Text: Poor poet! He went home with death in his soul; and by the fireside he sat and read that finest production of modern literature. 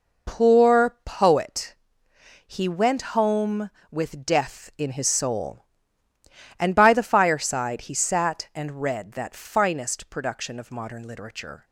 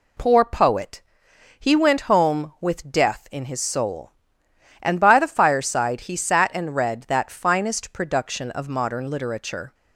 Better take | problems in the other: neither | none

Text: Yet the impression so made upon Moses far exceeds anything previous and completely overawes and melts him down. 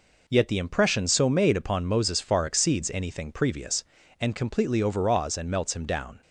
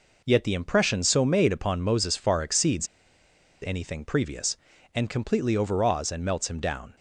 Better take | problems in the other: first | pauses between "exceeds" and "anything"; noticeable; at 2.8 s; 0.76 s long

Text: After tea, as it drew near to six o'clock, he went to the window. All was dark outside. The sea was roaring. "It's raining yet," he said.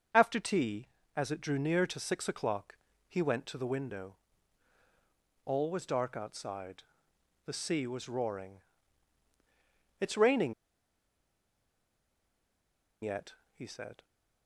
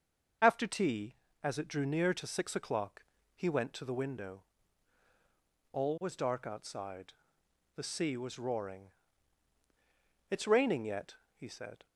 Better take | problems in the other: second | starts louder than the rest; until 1.4 s; 6.5 dB; also in the second // pauses between "raining" and "yet"; strong; at 10.5 s; 2.4 s long

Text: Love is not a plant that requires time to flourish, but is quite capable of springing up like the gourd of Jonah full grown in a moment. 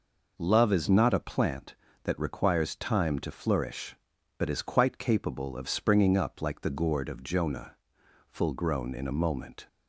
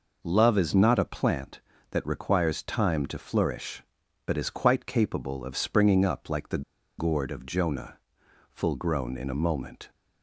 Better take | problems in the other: first | pauses between "the" and "gourd"; at 6.6 s; 0.37 s long // pauses between "Jonah" and "full"; noticeable; at 7.9 s; 0.54 s long; noticeable in the first

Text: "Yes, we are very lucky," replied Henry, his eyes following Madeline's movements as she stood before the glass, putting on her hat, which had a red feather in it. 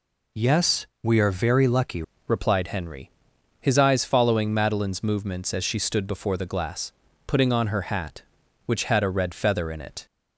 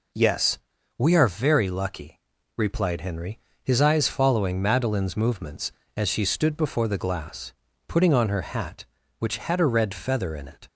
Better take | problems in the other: second | changes voice at "replied"; from 2.2 s on; 7.8 s long

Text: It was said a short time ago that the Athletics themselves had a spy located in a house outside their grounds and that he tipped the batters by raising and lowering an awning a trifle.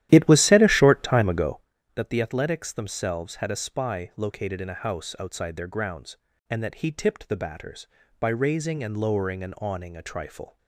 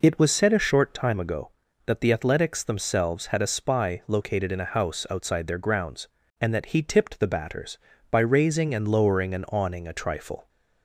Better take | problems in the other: second | starts louder than the rest; strong; until 1.7 s; 12.5 dB

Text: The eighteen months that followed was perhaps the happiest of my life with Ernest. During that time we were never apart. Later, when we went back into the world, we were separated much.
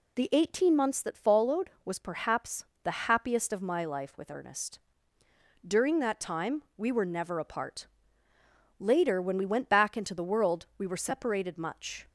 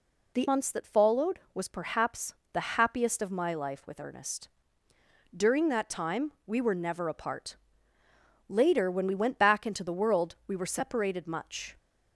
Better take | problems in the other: first | skips "eighteen"; at 0.4 s // pauses between "perhaps" and "the"; slight; at 2.3 s; 0.18 s long; slight in the first

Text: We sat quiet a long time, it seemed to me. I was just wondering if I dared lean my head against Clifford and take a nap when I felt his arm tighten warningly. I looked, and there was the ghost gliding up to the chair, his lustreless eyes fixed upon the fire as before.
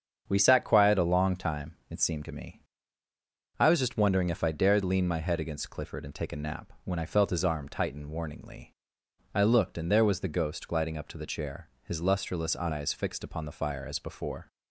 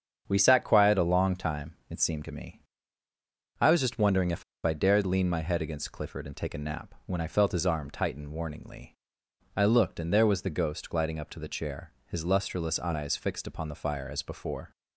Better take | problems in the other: first | starts louder than the rest; strong; until 1.2 s; 7.5 dB; strong in the first // pauses between "if" and "I"; slight; at 4.4 s; 0.20 s long

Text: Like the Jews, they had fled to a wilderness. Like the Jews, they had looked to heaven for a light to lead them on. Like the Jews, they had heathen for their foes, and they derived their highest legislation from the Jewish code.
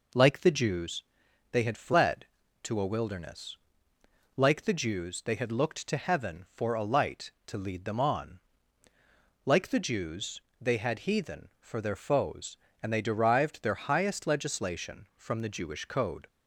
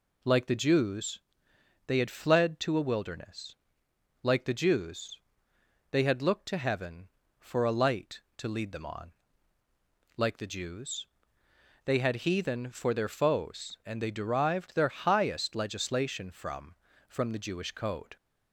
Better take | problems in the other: first | says "from" twice; at 17.0 s

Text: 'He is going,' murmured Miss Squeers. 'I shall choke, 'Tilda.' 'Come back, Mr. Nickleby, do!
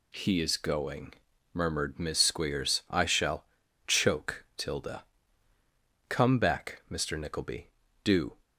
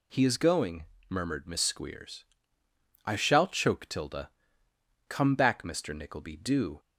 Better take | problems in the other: second | pauses between "shall" and "choke"; at 3.4 s; 0.43 s long

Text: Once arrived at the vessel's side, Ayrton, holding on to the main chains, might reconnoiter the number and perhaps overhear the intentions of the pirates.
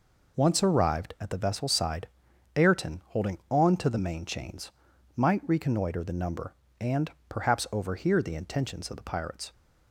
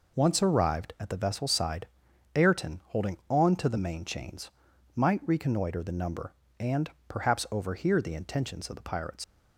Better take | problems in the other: first | pauses between "and" and "perhaps"; slight; at 6.8 s; 0.20 s long; slight in the first // leaves "pirates" unfinished; at 9.2 s; 75 ms

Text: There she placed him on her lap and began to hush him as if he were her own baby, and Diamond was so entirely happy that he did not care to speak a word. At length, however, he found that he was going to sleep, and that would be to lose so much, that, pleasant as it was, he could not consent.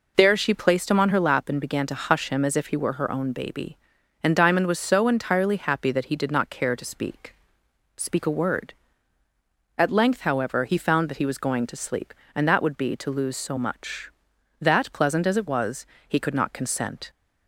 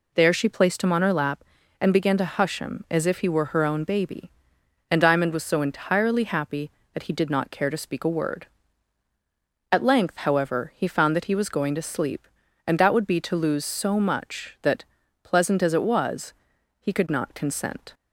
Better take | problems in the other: second | says "speak" twice; at 7.9 s

